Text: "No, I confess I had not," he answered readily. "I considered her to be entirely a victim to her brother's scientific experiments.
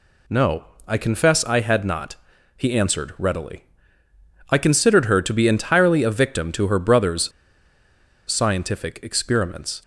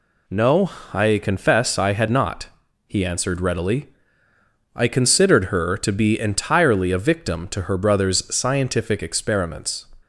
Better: second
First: pauses between "brother's" and "scientific"; at 7.3 s; 0.98 s long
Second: none

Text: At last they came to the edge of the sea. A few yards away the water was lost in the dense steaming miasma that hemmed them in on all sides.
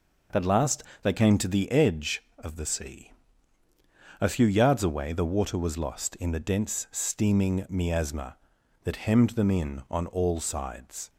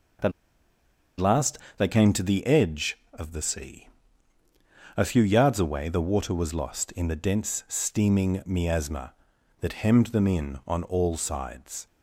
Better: first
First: pauses between "last" and "they"; slight; at 0.8 s; 0.20 s long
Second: pauses between "At" and "last"; noticeable; at 0.3 s; 0.88 s long // pauses between "last" and "they"; slight; at 1.5 s; 0.20 s long

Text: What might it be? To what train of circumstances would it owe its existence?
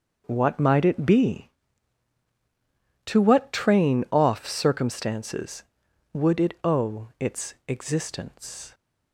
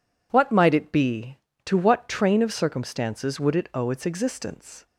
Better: second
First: starts louder than the rest; until 1.2 s; 6.5 dB // says "off" for "of"; at 4.0 s // pauses between "its" and "existence"; slight; at 7.5 s; 0.16 s long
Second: none

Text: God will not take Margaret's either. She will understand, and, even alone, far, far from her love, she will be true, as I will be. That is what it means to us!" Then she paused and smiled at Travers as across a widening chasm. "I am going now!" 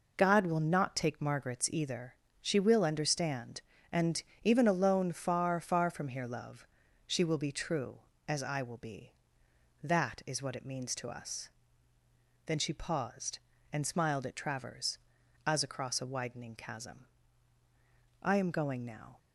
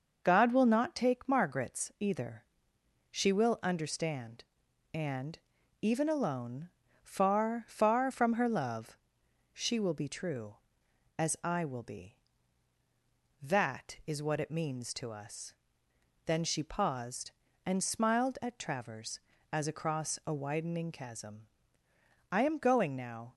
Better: second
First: says "here" for "her"; at 6.0 s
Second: none

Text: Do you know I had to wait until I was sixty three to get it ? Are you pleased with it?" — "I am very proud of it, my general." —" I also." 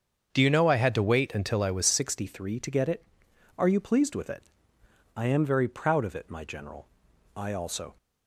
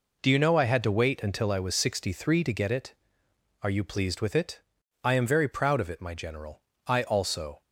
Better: second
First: starts louder than the rest; strong; until 1.3 s; 7.5 dB // changes voice at "sixty"; from 1.8 s on; 6.1 s long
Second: none

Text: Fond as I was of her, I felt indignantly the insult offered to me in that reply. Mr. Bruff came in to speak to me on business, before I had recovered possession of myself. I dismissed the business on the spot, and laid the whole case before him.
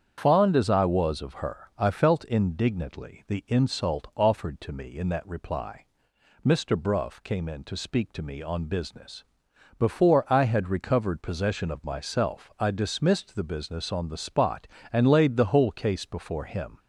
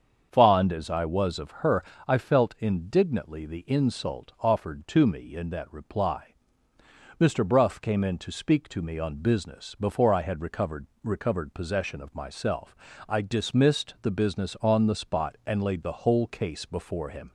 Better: first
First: starts louder than the rest; strong; until 1.1 s; 8 dB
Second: starts louder than the rest; until 1.3 s; 7 dB // says "recovered" twice; at 11.0 s

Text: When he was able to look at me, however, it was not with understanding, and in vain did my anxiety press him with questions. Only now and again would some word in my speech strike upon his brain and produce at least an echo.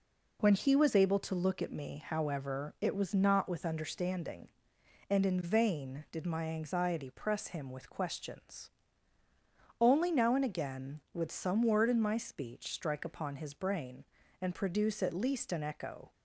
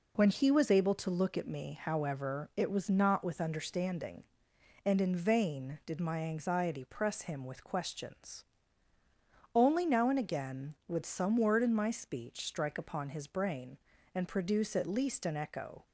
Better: neither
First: none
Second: none

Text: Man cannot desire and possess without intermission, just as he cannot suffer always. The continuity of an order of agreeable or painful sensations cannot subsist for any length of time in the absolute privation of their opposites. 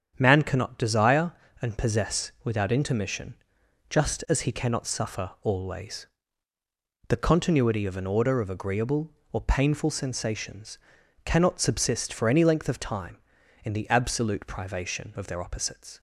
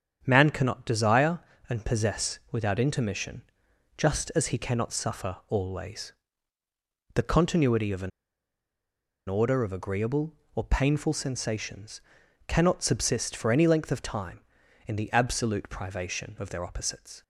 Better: first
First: starts louder than the rest; strong; until 1.1 s; 8 dB // pauses between "sensations" and "cannot"; noticeable; at 10.7 s; 0.48 s long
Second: starts louder than the rest; strong; until 1.2 s; 8 dB // pauses between "an" and "order"; at 8.1 s; 1.1 s long // pauses between "sensations" and "cannot"; noticeable; at 12.0 s; 0.48 s long

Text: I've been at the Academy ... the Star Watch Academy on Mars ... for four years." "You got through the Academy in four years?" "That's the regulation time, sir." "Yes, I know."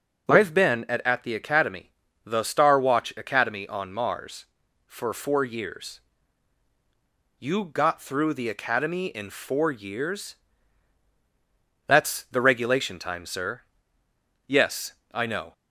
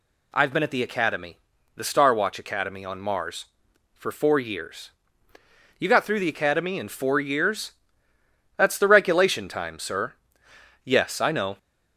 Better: second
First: says "at" twice; at 1.0 s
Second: none

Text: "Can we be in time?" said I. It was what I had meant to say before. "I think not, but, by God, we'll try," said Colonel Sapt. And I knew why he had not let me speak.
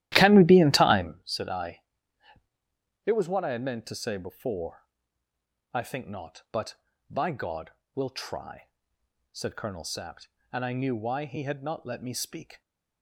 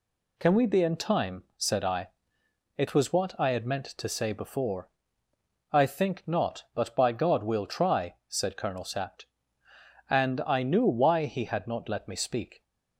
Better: second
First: starts louder than the rest; strong; until 1.1 s; 14 dB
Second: none

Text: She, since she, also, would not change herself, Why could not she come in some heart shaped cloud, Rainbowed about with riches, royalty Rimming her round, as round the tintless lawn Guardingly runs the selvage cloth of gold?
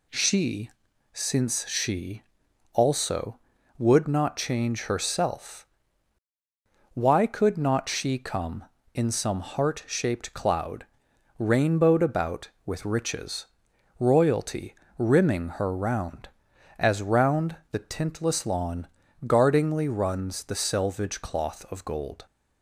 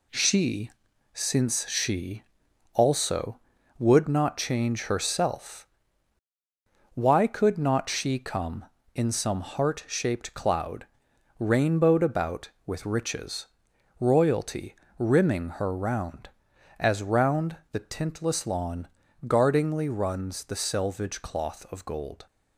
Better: first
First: pauses between "royalty" and "Rimming"; slight; at 14.7 s; 0.24 s long // pauses between "lawn" and "Guardingly"; at 18.8 s; 0.40 s long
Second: gets quieter; noticeable; throughout; 5.5 dB // pauses between "royalty" and "Rimming"; slight; at 14.7 s; 0.24 s long // pauses between "lawn" and "Guardingly"; at 18.8 s; 0.40 s long

